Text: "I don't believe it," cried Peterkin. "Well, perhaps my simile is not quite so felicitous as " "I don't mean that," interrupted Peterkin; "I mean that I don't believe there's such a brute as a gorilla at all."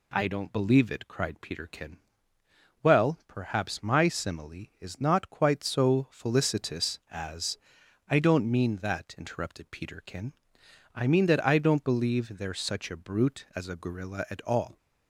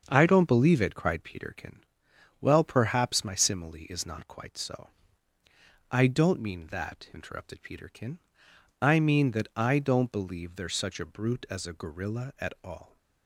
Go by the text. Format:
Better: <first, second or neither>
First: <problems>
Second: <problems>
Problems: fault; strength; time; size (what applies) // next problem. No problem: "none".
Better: first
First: none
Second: starts louder than the rest; until 1.0 s; 7 dB // skips "felicitous as"; at 5.1 s